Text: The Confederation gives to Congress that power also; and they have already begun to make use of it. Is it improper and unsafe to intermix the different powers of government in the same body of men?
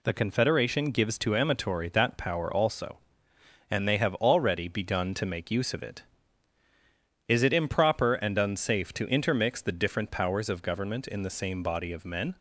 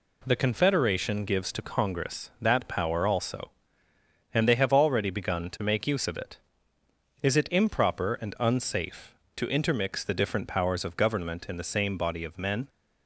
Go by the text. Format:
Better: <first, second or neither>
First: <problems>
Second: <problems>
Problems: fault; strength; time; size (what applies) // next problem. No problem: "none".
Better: second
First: says "Amatory" for "Congress"; at 1.3 s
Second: none